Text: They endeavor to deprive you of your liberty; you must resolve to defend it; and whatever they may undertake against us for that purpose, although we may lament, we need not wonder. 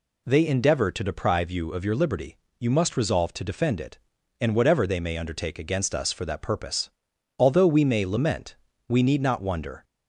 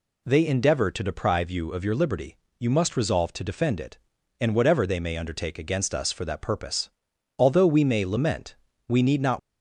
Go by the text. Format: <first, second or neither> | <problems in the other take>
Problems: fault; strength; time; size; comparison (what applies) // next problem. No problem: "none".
first | stops before "wonder"; at 9.3 s